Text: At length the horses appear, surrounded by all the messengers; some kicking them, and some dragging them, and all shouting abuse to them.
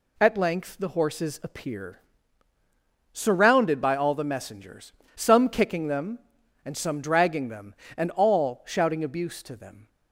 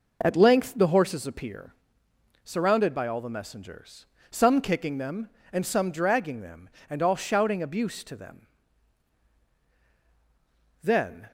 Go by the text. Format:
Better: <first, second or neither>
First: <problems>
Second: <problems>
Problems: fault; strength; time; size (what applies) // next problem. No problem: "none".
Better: first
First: none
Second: goes on to say "Then"; slight; from 10.8 s on; 0.48 s long